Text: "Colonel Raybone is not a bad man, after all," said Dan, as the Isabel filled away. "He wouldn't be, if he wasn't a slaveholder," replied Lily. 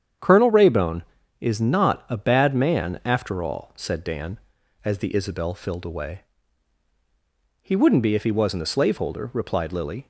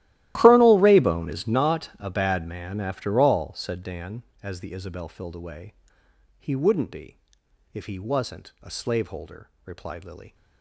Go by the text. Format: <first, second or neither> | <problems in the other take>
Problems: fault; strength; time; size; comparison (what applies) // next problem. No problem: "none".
first | gets quieter; strong; throughout; 19.5 dB // starts louder than the rest; strong; until 1.3 s; 15 dB; strong in the first